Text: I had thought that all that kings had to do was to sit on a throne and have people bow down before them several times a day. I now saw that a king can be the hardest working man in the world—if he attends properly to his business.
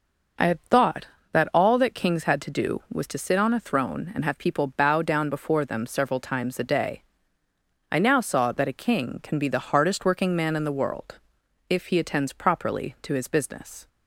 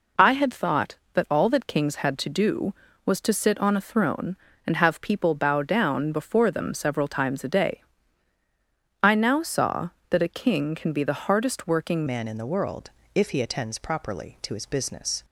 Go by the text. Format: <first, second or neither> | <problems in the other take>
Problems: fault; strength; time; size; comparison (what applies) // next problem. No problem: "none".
first | changes voice at "man"; from 12.0 s on; 3.2 s long